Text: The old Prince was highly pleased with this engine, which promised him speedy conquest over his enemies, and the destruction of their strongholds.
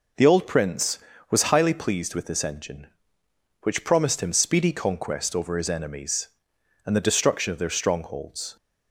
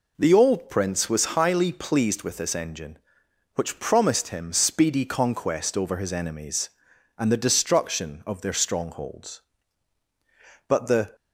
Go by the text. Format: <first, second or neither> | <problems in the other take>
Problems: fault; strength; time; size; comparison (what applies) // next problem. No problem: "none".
first | goes on to say "But the"; slight; from 10.6 s on; 0.48 s long